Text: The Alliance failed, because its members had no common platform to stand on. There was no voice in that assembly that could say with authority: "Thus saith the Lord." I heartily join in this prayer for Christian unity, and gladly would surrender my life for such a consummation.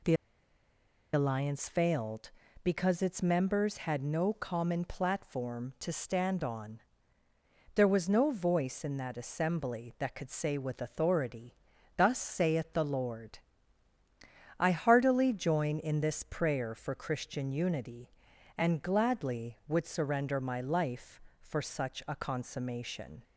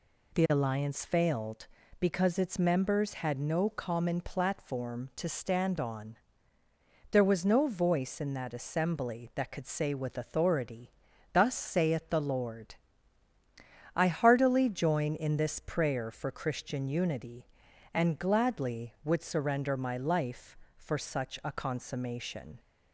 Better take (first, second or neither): second